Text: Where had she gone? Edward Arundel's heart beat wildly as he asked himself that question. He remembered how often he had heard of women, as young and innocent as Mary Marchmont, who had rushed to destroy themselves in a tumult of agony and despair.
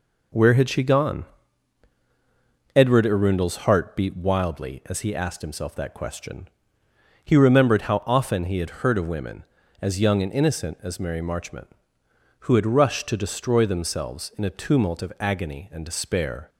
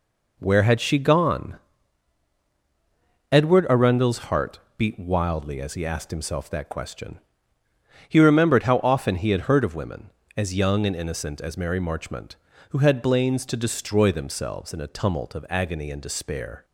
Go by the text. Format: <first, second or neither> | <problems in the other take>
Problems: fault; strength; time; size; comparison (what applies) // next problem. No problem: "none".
first | pauses between "heart" and "beat"; slight; at 4.6 s; 0.16 s long // says "blains" for "rushed"; at 13.0 s